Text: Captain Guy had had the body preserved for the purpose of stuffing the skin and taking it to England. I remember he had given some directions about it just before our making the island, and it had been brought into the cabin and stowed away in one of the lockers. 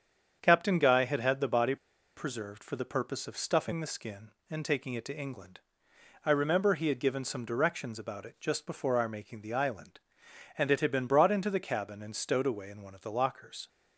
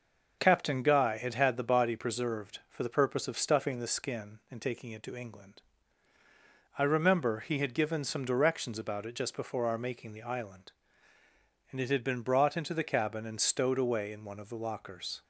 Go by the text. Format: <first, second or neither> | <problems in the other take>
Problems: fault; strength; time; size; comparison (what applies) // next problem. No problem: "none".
second | starts louder than the rest; strong; until 1.4 s; 7.5 dB // pauses between "body" and "preserved"; at 1.7 s; 0.41 s long